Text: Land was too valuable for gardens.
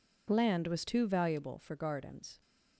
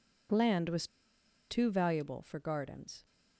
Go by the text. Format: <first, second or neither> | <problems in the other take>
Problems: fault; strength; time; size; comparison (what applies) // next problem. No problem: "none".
first | pauses between "was" and "too"; noticeable; at 0.8 s; 0.62 s long